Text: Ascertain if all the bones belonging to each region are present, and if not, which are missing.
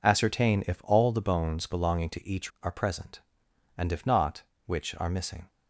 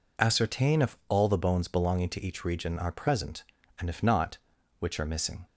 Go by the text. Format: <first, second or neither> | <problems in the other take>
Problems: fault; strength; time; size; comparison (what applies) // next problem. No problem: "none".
second | skips "region"; at 2.5 s